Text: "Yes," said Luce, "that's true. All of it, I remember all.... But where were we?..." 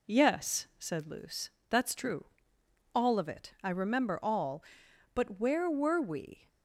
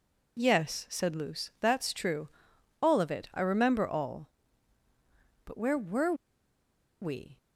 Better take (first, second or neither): first